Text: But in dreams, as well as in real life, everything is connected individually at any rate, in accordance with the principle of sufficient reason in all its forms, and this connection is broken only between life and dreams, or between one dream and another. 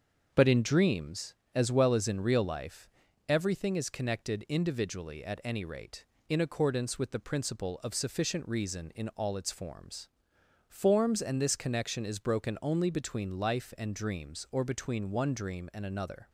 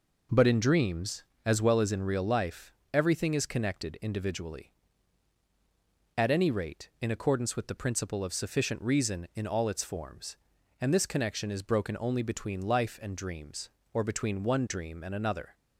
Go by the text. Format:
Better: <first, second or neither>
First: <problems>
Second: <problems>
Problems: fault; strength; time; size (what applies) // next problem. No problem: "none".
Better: second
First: starts louder than the rest; until 1.3 s; 6.5 dB // says "forms" twice; at 10.6 s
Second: none